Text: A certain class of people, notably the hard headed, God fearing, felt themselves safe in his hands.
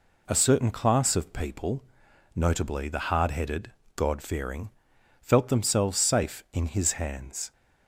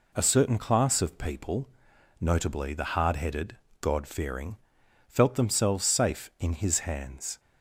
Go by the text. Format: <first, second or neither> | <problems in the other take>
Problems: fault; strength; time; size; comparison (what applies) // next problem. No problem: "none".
neither | none